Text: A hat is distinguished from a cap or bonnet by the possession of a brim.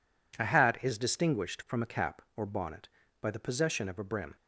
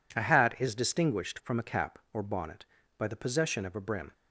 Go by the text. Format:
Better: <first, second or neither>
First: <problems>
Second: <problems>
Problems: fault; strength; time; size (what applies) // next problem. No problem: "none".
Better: neither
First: none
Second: none